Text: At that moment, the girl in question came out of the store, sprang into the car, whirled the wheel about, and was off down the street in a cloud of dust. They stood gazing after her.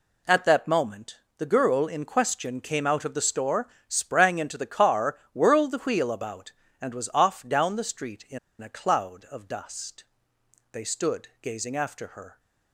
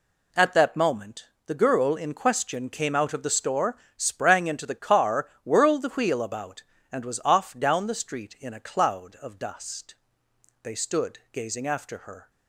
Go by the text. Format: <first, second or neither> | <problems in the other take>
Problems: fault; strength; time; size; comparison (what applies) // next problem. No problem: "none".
second | pauses between "in" and "a"; slight; at 8.3 s; 0.22 s long